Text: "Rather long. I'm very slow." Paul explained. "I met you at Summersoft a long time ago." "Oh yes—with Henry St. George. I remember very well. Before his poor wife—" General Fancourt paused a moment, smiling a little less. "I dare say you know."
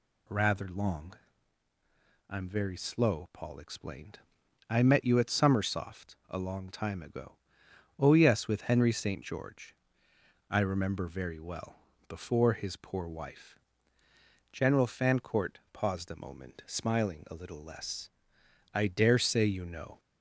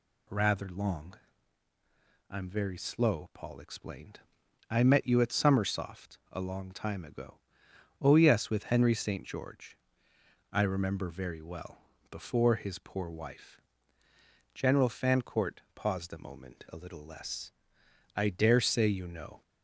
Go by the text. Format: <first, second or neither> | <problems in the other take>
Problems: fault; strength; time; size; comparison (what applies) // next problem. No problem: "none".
first | skips "smiling"; at 16.6 s